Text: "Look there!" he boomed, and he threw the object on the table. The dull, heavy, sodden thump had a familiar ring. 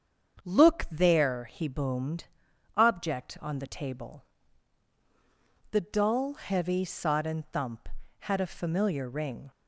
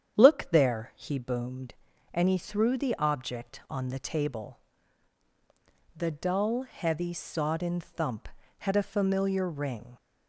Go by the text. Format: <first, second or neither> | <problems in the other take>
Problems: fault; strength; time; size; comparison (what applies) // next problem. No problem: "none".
second | starts louder than the rest; strong; until 1.4 s; 7 dB; strong in the second // skips "and he threw the"; at 2.5 s